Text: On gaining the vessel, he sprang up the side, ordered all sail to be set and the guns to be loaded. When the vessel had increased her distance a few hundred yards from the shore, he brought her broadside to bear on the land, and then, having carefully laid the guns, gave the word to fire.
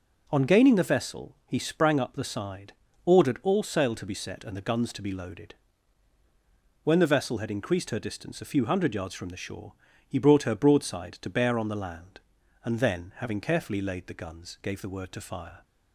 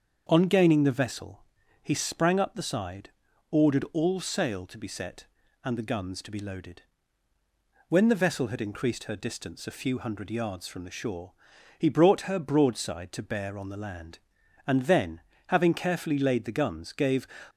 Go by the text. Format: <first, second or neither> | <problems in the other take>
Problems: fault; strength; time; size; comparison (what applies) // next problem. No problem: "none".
first | starts louder than the rest; until 1.3 s; 7 dB // stops before "the word to fire"; at 17.4 s